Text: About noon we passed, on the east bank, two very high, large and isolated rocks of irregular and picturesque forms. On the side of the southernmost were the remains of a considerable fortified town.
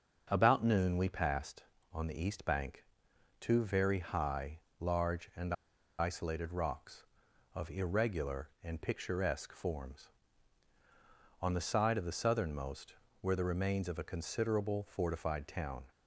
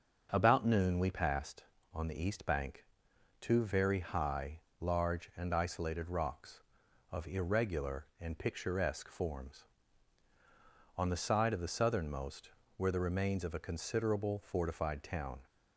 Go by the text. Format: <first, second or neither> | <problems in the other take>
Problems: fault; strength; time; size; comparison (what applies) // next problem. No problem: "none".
second | starts louder than the rest; until 1.3 s; 6.5 dB; also in the second // pauses between "and" and "isolated"; at 5.5 s; 0.44 s long